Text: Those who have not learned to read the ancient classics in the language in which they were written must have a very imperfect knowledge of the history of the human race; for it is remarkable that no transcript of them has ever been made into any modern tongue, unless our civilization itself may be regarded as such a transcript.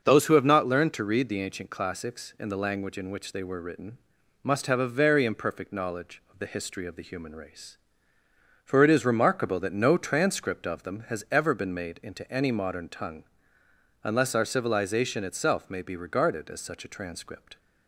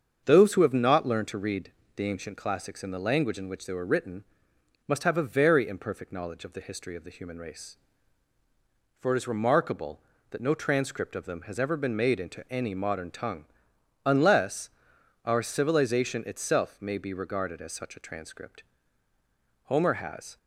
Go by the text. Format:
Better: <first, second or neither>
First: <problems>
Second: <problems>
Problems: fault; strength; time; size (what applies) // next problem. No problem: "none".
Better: first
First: starts louder than the rest; until 1.0 s; 6.5 dB // pauses between "written" and "must"; at 3.9 s; 0.44 s long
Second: starts louder than the rest; strong; until 1.2 s; 7 dB // pauses between "read" and "the"; slight; at 1.7 s; 0.24 s long // pauses between "written" and "must"; noticeable; at 4.2 s; 0.64 s long // pauses between "unless" and "our"; noticeable; at 14.6 s; 0.56 s long // goes on to say "Homer has"; noticeable; from 19.6 s on; 0.72 s long